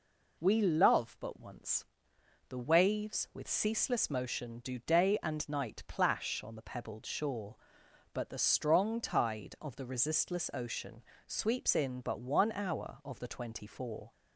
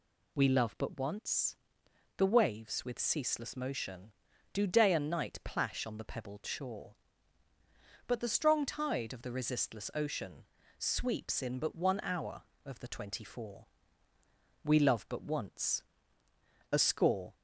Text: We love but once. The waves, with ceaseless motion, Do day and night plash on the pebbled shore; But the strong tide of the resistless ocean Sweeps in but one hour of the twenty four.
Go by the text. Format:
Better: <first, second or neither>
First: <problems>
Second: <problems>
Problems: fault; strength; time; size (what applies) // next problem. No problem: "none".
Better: first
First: pauses between "ocean" and "Sweeps"; slight; at 11.0 s; 0.24 s long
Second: pauses between "ocean" and "Sweeps"; slight; at 10.4 s; 0.34 s long // goes on to say "We love but once A score"; strong; from 14.6 s on; 2.7 s long